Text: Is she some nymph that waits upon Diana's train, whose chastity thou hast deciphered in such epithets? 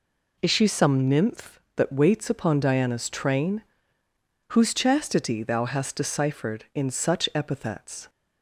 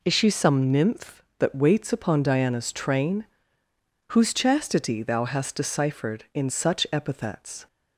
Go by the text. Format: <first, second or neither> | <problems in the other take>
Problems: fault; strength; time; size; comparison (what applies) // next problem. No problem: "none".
neither | none